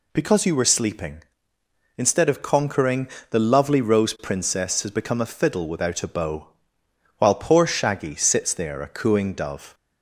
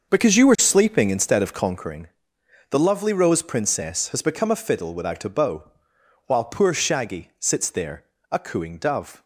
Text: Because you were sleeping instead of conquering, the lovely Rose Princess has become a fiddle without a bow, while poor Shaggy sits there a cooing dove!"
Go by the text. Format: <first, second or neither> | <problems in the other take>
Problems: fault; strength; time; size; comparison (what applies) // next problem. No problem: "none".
first | starts louder than the rest; until 1.9 s; 6.5 dB // pauses between "there" and "a"; slight; at 8.0 s; 0.26 s long